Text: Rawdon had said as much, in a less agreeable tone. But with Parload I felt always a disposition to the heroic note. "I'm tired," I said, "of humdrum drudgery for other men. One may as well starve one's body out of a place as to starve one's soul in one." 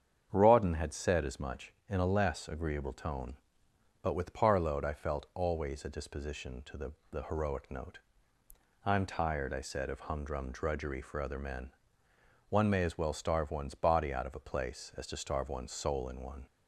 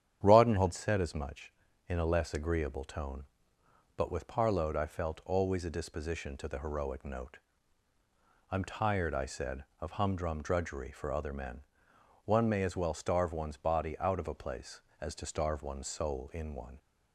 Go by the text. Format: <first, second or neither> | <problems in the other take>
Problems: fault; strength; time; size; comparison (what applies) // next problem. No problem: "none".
second | starts louder than the rest; strong; until 1.3 s; 8 dB; strong in the second // says "the" twice; at 7.0 s